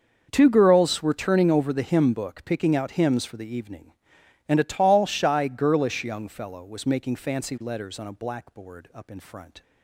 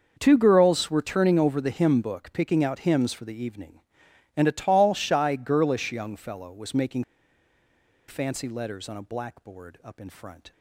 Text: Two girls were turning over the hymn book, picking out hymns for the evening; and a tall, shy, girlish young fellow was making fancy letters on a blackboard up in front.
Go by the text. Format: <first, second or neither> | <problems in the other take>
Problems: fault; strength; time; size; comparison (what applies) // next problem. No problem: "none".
first | starts louder than the rest; until 1.2 s; 6.5 dB; also in the first // pauses between "making" and "fancy"; at 7.0 s; 1.0 s long